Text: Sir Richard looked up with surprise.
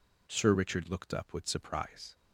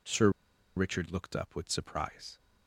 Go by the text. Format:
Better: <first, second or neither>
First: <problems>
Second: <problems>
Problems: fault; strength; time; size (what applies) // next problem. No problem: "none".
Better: first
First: none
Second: pauses between "Sir" and "Richard"; noticeable; at 0.2 s; 0.47 s long